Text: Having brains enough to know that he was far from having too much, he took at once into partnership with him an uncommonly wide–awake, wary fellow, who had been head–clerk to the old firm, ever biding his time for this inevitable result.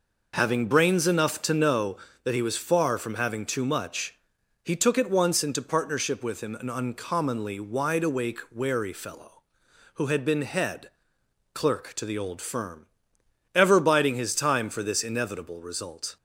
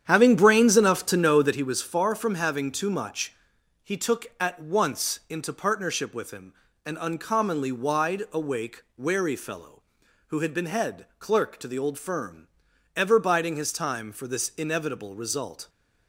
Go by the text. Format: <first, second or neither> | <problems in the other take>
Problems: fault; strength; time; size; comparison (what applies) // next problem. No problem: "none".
first | starts louder than the rest; strong; until 1.6 s; 9 dB // pauses between "him" and "an"; slight; at 6.5 s; 0.32 s long